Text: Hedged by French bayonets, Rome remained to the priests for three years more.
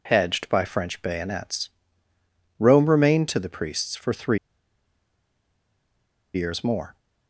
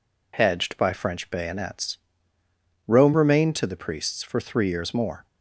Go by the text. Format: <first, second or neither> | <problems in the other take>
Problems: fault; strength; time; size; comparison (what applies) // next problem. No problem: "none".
second | pauses between "three" and "years"; strong; at 4.3 s; 1.9 s long